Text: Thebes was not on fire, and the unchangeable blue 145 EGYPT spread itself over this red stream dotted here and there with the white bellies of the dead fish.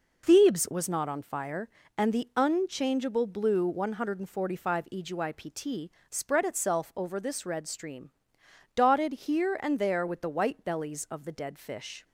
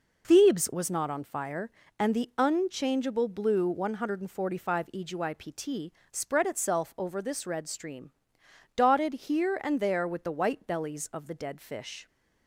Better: neither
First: pauses between "EGYPT" and "spread"; slight; at 5.9 s; 0.18 s long // pauses between "stream" and "dotted"; noticeable; at 8.0 s; 0.66 s long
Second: pauses between "EGYPT" and "spread"; slight; at 5.9 s; 0.18 s long // pauses between "stream" and "dotted"; noticeable; at 8.0 s; 0.66 s long

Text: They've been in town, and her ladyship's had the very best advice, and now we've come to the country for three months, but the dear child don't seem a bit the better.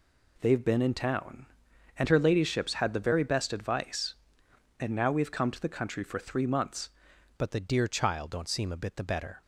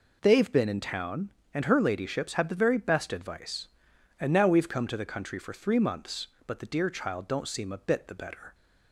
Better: second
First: changes voice at "but"; from 7.3 s on; 2.1 s long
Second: none

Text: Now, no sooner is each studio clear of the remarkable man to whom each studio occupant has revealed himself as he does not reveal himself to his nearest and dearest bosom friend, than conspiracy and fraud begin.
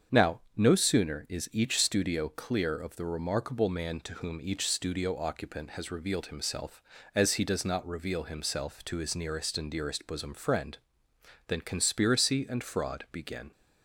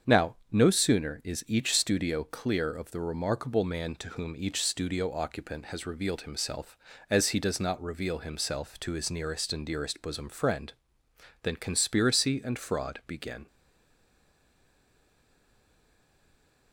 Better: first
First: starts louder than the rest; strong; until 1.3 s; 7 dB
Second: starts louder than the rest; strong; until 1.2 s; 7 dB // stays silent after the last word; strong; from 13.4 s on; 3.3 s long

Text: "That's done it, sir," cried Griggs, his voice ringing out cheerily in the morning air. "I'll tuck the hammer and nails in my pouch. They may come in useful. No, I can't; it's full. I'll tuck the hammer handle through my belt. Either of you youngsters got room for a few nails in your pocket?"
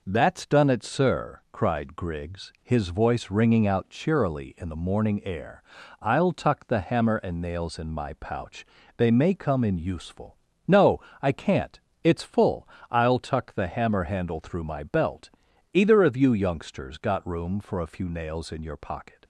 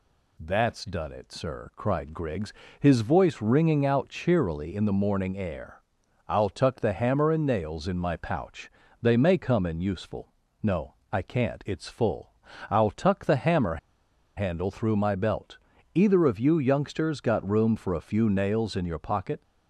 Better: first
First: none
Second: pauses between "hammer" and "handle"; noticeable; at 13.7 s; 0.59 s long

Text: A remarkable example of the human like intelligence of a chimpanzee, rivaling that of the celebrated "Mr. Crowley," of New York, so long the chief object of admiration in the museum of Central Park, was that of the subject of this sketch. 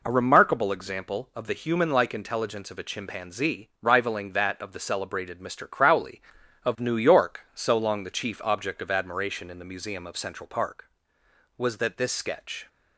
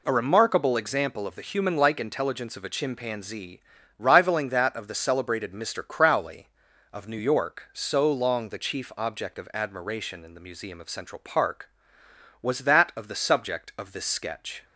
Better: second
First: skips "of the subject of"; at 11.9 s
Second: none

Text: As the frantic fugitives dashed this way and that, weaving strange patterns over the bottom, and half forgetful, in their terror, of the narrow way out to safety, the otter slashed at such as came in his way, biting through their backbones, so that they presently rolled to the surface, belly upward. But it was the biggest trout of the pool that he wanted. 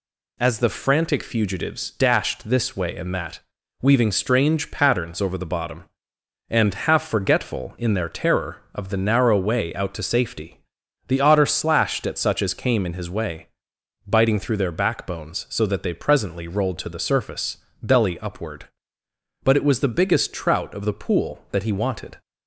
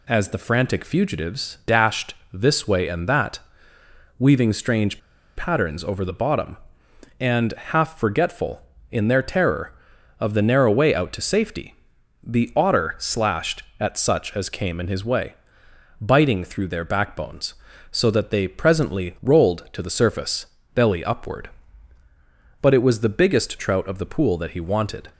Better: first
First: none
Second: pauses between "dashed" and "this"; slight; at 2.1 s; 0.18 s long // pauses between "strange" and "patterns"; at 4.9 s; 0.37 s long

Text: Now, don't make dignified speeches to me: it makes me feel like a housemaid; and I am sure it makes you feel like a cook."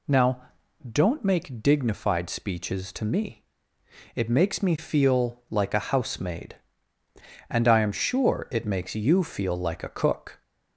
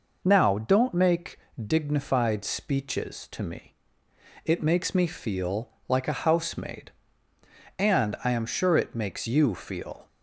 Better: first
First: none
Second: pauses between "make" and "dignified"; slight; at 1.3 s; 0.26 s long // pauses between "feel" and "like"; slight; at 5.6 s; 0.18 s long // stops before "like a cook"; at 10.0 s

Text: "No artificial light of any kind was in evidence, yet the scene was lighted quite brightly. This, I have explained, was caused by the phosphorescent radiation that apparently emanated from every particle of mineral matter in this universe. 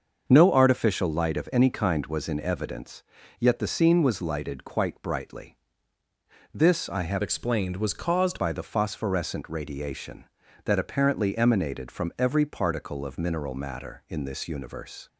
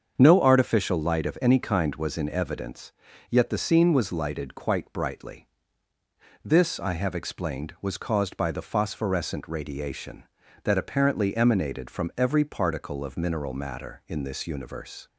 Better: second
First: starts louder than the rest; until 1.2 s; 6.5 dB // changes voice from "explained" to "caused"; from 7.2 to 8.3 s; 1.1 s long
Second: starts louder than the rest; strong; until 1.1 s; 7 dB

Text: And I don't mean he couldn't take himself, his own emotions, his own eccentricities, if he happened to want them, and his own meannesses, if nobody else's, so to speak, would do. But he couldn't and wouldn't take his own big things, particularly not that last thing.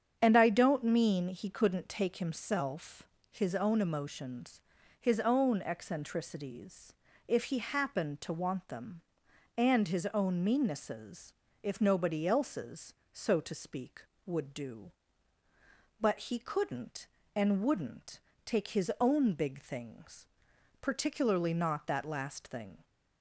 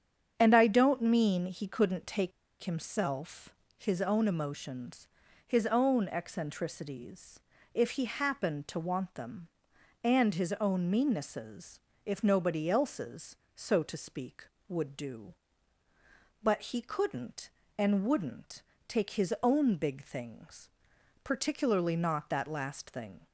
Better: first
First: starts louder than the rest; strong; until 1.2 s; 8 dB // pauses between "wouldn't" and "take"; slight; at 18.1 s; 0.26 s long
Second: starts louder than the rest; strong; until 1.3 s; 8 dB // pauses between "take" and "himself"; slight; at 2.3 s; 0.31 s long // pauses between "wouldn't" and "take"; slight; at 18.6 s; 0.26 s long

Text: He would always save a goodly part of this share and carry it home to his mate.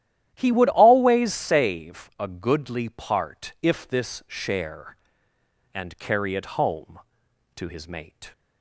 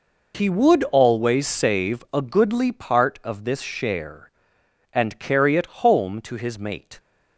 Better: second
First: starts louder than the rest; strong; until 1.3 s; 12 dB // says "if" for "of"; at 3.6 s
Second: none

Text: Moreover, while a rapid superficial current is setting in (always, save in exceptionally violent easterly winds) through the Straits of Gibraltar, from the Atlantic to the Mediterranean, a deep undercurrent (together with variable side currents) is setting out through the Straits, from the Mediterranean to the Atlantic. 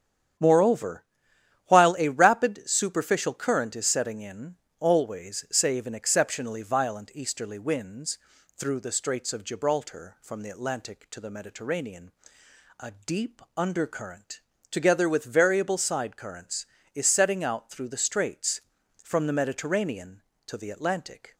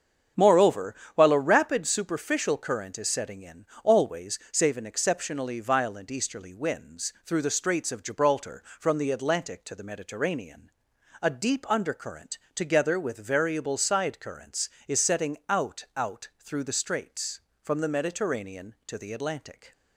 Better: first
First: starts louder than the rest; strong; until 2.0 s; 9 dB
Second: starts louder than the rest; strong; until 1.5 s; 7.5 dB // says "out" twice; at 15.9 s

